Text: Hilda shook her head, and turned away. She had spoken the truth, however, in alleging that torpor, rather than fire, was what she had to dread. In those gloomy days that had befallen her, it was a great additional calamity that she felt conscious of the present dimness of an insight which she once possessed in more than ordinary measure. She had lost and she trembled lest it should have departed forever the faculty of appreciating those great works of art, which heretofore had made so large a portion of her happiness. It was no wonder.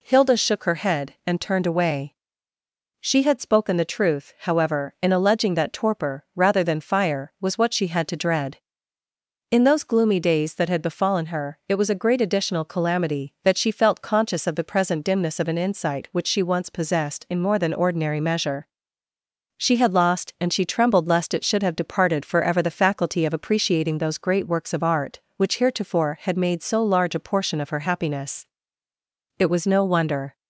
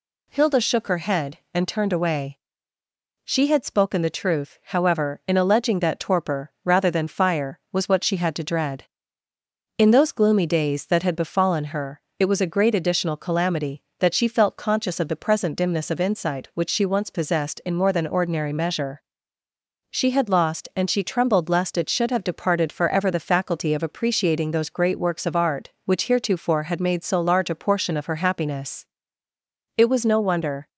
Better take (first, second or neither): first